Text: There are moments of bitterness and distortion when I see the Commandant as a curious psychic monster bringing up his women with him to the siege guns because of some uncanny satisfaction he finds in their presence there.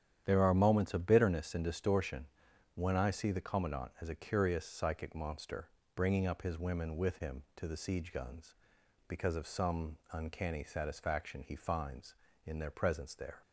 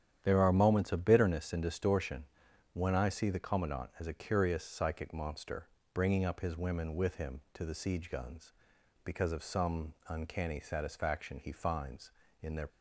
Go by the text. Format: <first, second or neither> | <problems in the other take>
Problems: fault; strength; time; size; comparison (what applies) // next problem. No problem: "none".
first | starts louder than the rest; strong; until 1.2 s; 9.5 dB; strong in the first // pauses between "distortion" and "when"; noticeable; at 2.2 s; 0.48 s long; noticeable in the first // pauses between "monster" and "bringing"; slight; at 5.6 s; 0.26 s long; slight in the first // stops before "presence there"; at 12.6 s